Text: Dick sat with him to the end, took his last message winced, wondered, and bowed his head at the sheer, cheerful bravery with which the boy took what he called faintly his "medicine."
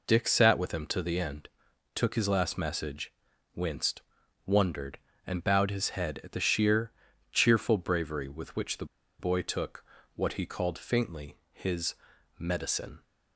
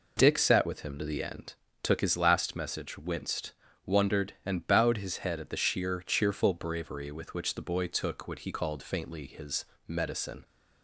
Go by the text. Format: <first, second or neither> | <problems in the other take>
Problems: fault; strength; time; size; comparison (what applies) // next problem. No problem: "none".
second | pauses between "message" and "winced"; at 3.1 s; 0.44 s long // pauses between "the" and "boy"; slight; at 8.8 s; 0.33 s long // pauses between "took" and "what"; slight; at 9.8 s; 0.30 s long // pauses between "faintly" and "his"; slight; at 11.3 s; 0.16 s long // pauses between "his" and "medicine"; at 11.9 s; 0.44 s long; slight in the second